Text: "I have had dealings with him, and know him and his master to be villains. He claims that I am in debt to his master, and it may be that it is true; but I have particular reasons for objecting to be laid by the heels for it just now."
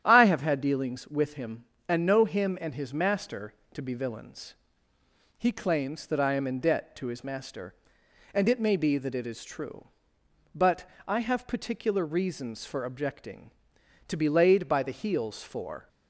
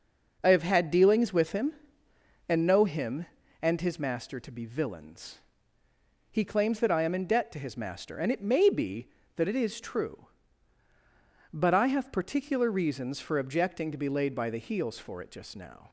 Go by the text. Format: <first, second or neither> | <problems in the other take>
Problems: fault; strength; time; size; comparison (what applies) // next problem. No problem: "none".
second | starts louder than the rest; strong; until 1.0 s; 10.5 dB // pauses between "but" and "I"; slight; at 10.8 s; 0.22 s long // stops before "it just now"; at 15.8 s